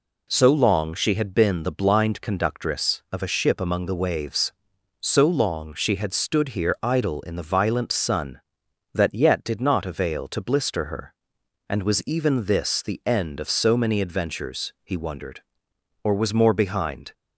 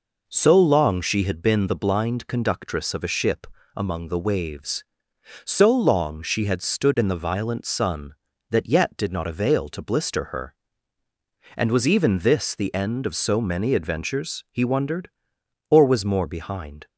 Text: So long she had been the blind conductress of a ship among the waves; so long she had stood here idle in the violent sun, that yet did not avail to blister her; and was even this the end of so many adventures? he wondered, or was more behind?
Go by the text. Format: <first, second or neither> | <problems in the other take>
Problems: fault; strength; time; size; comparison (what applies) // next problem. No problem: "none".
first | pauses between "ship" and "among"; slight; at 3.4 s; 0.30 s long // skips "here idle"; at 6.9 s